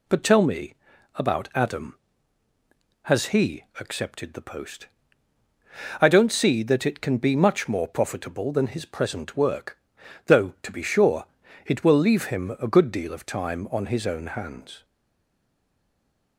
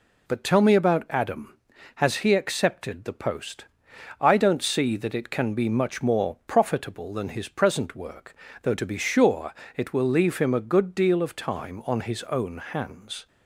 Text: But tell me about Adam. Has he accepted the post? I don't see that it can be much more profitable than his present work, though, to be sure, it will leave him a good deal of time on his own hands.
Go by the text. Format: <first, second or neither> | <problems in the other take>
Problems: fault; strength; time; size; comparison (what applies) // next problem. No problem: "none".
second | pauses between "me" and "about"; at 0.7 s; 0.40 s long // stays silent after the last word; noticeable; from 14.8 s on; 1.5 s long